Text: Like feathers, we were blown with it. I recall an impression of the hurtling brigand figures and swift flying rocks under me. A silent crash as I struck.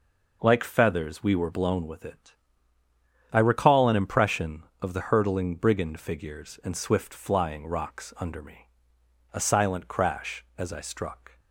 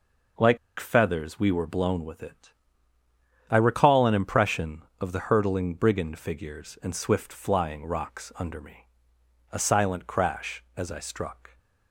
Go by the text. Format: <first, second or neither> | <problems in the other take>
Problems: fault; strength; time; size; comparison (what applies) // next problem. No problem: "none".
first | pauses between "Like" and "feathers"; slight; at 0.5 s; 0.21 s long